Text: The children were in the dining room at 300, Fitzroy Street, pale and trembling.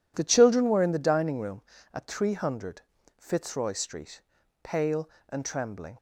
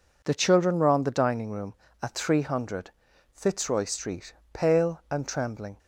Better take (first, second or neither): first